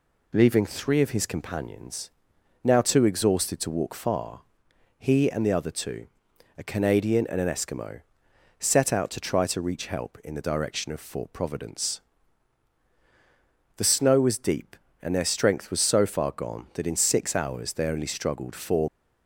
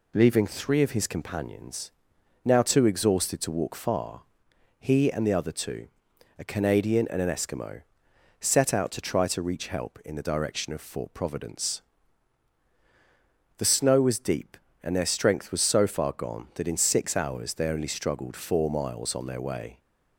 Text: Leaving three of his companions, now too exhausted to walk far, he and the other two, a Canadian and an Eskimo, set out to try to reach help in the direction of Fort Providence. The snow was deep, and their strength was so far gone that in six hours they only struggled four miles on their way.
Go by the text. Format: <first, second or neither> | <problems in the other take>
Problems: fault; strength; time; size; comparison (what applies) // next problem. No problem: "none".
second | stops before "miles on their way"; at 18.8 s